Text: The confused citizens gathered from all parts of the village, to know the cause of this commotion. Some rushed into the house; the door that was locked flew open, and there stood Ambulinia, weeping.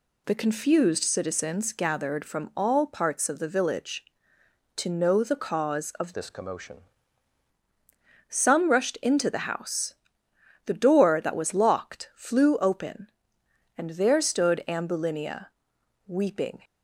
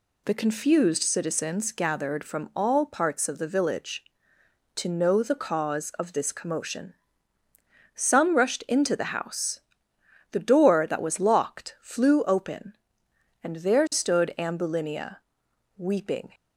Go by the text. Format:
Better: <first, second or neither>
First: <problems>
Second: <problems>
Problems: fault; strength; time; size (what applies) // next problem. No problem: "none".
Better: second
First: changes voice from "this" to "commotion"; from 6.1 to 6.7 s; 0.6 s long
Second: none